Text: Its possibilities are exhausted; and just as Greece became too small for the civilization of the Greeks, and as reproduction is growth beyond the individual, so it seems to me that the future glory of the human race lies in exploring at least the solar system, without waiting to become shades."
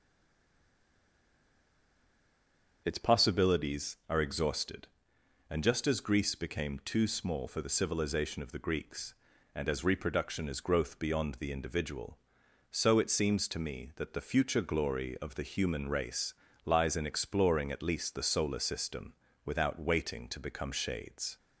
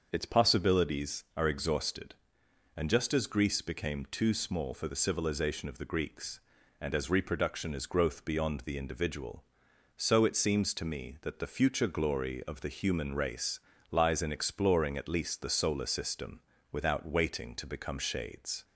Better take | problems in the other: second | stays silent before the first word; strong; until 2.8 s; 2.8 s long // starts louder than the rest; until 3.8 s; 6.5 dB; also in the second // pauses between "race" and "lies"; slight; at 16.3 s; 0.32 s long; slight in the second

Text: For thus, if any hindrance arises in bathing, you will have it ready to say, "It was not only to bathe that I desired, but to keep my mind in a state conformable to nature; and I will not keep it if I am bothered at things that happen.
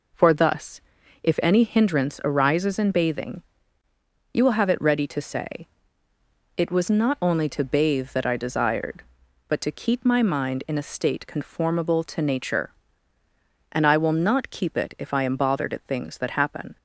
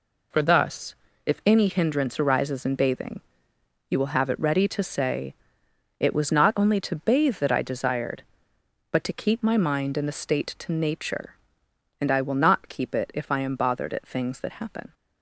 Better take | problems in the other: first | skips "conformable"; at 10.5 s

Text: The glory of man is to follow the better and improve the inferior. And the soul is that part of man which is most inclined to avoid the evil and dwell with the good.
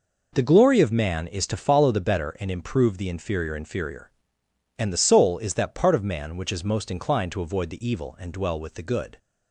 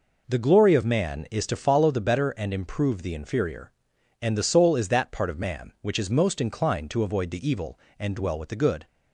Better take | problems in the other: second | says "inferior" twice; at 3.5 s

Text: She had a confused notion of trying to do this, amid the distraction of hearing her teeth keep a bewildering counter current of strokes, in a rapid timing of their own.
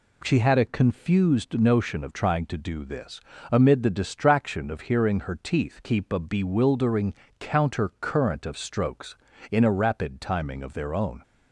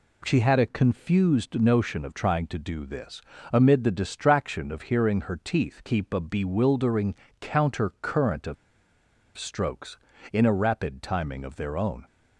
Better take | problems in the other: first | pauses between "bewildering" and "counter"; slight; at 7.1 s; 0.28 s long; slight in the first // pauses between "of" and "strokes"; noticeable; at 8.5 s; 0.81 s long

